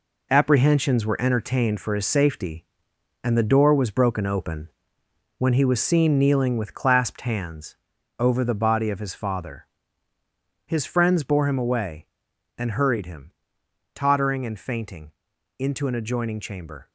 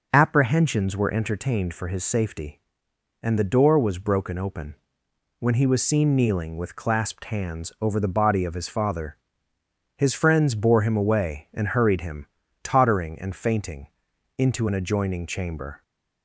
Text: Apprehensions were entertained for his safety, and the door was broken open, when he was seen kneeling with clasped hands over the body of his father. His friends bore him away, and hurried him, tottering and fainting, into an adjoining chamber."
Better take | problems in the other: second | gets quieter; strong; throughout; 8 dB // pauses between "hands" and "over"; at 7.7 s; 0.42 s long

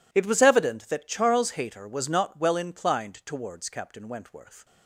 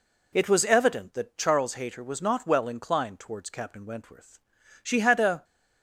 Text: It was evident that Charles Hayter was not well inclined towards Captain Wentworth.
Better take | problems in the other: first | goes on to say "She had a"; noticeable; from 4.8 s on; 0.62 s long

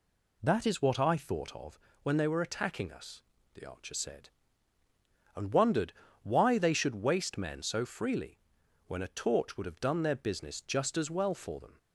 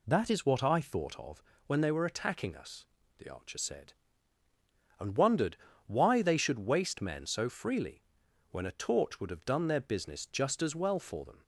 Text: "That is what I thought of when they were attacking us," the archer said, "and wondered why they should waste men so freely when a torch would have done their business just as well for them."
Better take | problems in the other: neither | pauses between "of" and "when"; slight; the same in both // pauses between "wondered" and "why"; slight; the same in both // pauses between "freely" and "when"; noticeable; the same in both

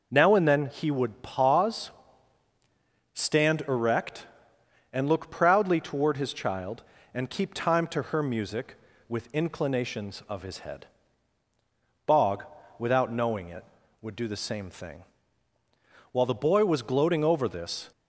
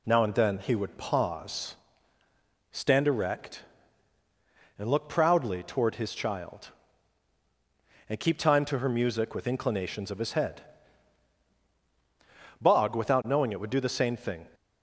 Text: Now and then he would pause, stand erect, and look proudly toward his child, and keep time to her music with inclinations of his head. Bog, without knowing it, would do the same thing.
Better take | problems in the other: second | goes on to say "While the boy was gloating over this"; strong; from 16.1 s on; 1.7 s long

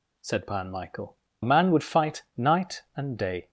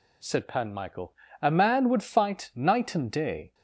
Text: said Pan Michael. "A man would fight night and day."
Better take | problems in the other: second | skips "A"; at 1.2 s

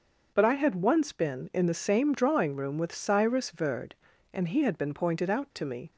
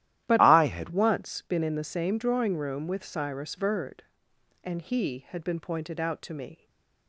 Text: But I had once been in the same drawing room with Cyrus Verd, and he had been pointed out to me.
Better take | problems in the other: first | starts louder than the rest; strong; until 1.2 s; 13 dB; also in the first // changes voice from "I" to "had"; from 0.3 to 0.8 s; 0.5 s long // stays silent after the last word; slight; from 6.5 s on; 0.5 s long

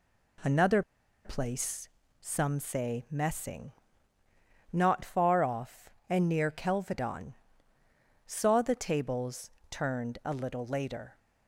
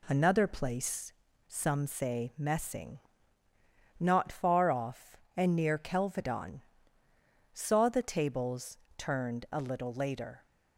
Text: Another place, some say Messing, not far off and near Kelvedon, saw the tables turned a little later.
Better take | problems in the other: second | pauses between "Another" and "place"; at 0.8 s; 0.43 s long // pauses between "tables" and "turned"; slight; at 9.4 s; 0.20 s long; slight in the second

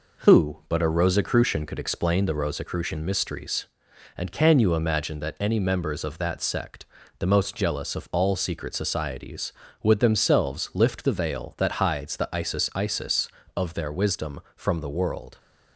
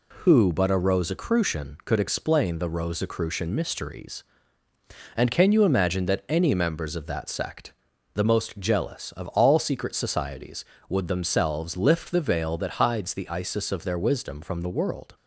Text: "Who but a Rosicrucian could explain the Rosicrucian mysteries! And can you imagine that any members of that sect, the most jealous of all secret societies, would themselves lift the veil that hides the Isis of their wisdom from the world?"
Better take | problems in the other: second | says "Isis" twice; at 12.7 s

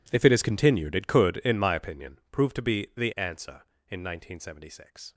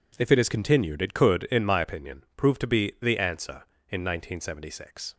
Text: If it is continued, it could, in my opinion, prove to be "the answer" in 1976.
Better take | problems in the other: second | gets quieter; strong; throughout; 19 dB

